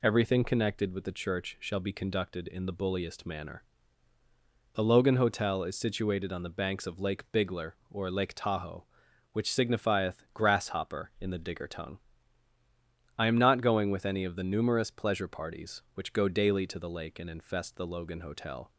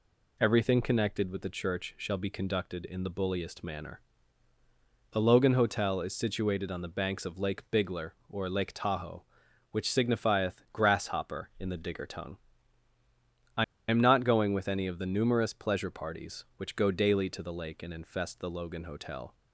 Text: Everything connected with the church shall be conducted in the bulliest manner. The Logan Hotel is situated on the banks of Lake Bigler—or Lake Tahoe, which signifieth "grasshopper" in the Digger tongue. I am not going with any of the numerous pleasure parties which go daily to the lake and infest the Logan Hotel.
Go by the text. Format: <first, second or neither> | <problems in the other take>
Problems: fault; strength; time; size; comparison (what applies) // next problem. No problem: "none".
first | pauses between "I" and "am"; slight; at 13.6 s; 0.25 s long